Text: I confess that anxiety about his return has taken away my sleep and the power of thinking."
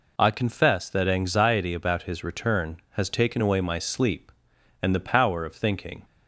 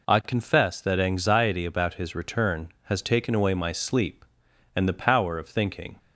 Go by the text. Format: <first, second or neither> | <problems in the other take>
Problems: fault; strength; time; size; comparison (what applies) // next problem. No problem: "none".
neither | none